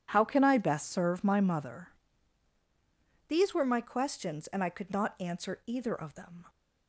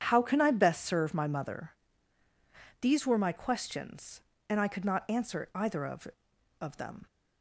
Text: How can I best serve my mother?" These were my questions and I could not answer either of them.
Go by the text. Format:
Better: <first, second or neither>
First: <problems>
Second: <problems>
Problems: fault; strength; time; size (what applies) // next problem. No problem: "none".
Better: first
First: none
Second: starts louder than the rest; strong; until 1.0 s; 8.5 dB // says "of" twice; at 6.6 s